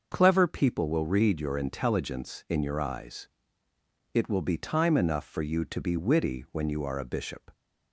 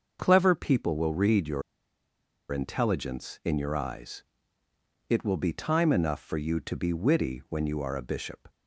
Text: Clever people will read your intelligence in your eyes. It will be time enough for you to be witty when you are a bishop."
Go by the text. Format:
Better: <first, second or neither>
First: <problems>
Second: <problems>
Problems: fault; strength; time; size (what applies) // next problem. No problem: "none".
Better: first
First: starts louder than the rest; until 1.1 s; 6 dB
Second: starts louder than the rest; until 1.2 s; 6 dB // pauses between "your" and "intelligence"; noticeable; at 1.6 s; 0.90 s long